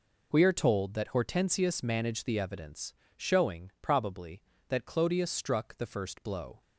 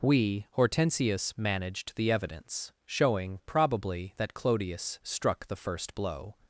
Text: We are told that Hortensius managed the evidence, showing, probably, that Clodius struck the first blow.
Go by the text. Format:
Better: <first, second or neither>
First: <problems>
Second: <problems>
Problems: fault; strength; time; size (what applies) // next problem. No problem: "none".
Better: first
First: none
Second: skips "are told that"; at 0.5 s